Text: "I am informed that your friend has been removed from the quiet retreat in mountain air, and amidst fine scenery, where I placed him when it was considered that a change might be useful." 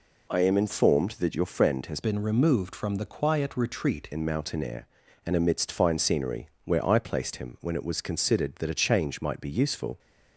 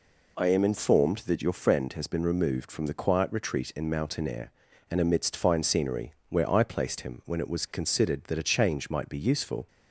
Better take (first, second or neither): second